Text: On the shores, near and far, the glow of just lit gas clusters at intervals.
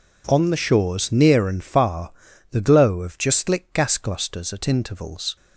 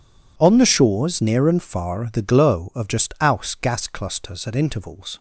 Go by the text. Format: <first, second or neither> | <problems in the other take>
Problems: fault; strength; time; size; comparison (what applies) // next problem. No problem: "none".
first | says "aus" for "lit"; at 3.2 s